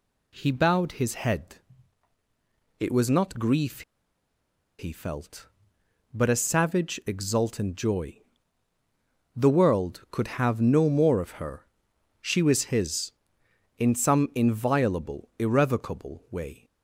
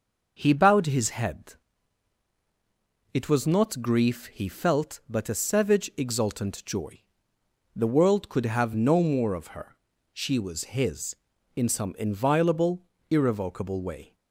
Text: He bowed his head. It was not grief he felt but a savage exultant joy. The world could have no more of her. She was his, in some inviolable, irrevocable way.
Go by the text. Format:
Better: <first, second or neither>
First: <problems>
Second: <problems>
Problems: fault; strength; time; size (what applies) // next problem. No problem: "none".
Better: second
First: pauses between "grief" and "he"; noticeable; at 3.8 s; 0.97 s long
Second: none